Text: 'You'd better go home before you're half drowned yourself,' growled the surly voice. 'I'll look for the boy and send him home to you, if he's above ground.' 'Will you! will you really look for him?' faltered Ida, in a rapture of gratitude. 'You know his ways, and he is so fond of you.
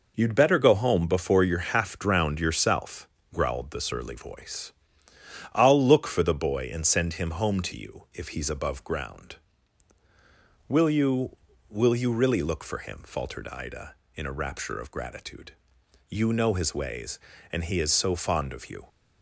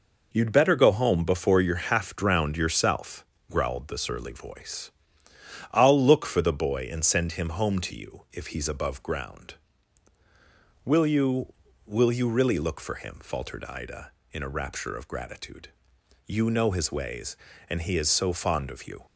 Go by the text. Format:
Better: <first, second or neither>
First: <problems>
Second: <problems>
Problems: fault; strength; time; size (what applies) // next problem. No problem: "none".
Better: neither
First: none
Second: none